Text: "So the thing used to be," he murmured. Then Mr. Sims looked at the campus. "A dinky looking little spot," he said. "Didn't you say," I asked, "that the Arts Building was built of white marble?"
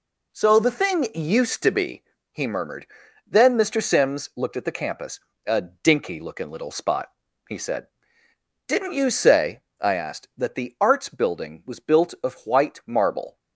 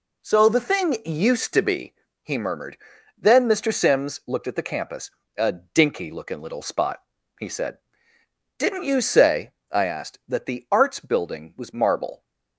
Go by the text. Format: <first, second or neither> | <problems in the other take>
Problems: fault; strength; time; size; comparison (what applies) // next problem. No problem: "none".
first | skips "built of white"; at 11.7 s